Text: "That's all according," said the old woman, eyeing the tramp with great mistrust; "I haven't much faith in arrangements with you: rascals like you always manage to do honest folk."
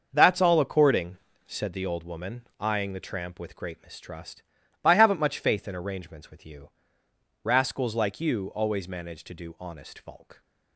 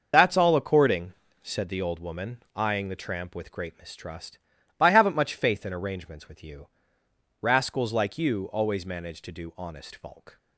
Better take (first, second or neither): first